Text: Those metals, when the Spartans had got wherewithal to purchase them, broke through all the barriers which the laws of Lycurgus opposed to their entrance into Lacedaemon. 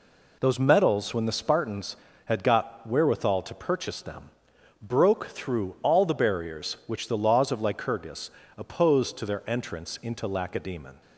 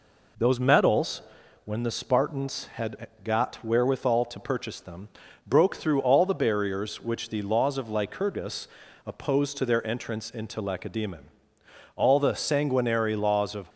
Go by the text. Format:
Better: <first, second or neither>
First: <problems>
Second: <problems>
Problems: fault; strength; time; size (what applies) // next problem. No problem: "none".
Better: first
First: pauses between "Lycurgus" and "opposed"; slight; at 8.3 s; 0.26 s long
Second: pauses between "had" and "got"; slight; at 3.0 s; 0.16 s long // pauses between "Lycurgus" and "opposed"; at 8.6 s; 0.40 s long // goes on to say "All the sanguinary laws of"; strong; from 11.9 s on; 1.7 s long